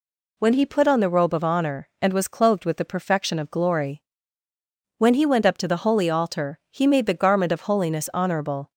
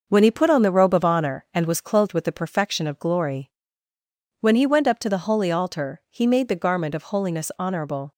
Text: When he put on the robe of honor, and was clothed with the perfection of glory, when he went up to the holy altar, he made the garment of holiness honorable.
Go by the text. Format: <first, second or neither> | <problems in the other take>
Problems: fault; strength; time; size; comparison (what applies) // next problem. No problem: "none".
first | gets quieter; noticeable; throughout; 5.5 dB